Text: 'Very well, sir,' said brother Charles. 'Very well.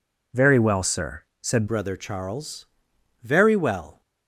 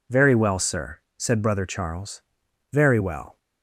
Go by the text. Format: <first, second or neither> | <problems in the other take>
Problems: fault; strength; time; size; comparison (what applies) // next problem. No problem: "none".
second | changes voice at "brother"; from 1.6 s on; 2.4 s long